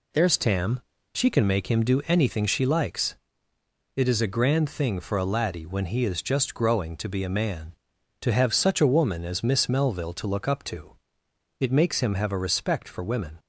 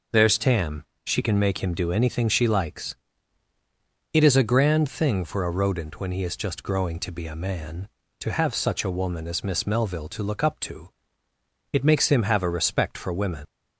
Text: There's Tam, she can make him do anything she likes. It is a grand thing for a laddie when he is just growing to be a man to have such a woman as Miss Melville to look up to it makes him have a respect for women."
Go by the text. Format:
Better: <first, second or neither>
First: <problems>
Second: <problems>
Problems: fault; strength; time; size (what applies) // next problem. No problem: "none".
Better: first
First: pauses between "to" and "it"; noticeable; at 10.9 s; 0.64 s long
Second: says "rodent" for "laddie"; at 5.5 s // pauses between "to" and "it"; noticeable; at 10.8 s; 0.82 s long